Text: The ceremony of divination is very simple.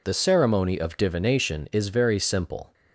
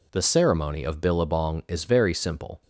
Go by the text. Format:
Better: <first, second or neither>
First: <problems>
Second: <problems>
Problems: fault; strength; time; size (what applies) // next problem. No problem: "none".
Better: first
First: none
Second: says "billabong" for "divination"; at 1.0 s